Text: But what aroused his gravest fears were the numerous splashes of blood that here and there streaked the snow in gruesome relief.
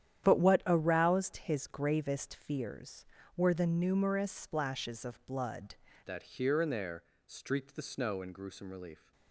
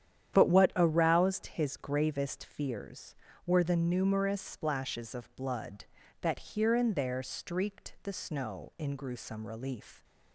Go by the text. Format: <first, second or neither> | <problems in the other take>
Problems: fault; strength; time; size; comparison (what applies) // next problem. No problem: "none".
second | starts louder than the rest; strong; until 1.2 s; 10 dB; strong in the second // changes voice at "that"; from 6.0 s on; 3.1 s long // pauses between "there" and "streaked"; slight; at 7.0 s; 0.22 s long